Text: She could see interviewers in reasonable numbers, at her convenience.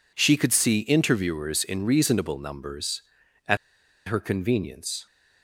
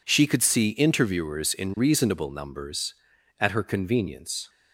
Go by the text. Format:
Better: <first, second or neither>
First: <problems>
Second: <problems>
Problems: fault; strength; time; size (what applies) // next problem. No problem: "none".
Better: second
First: pauses between "at" and "her"; noticeable; at 3.5 s; 0.50 s long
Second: none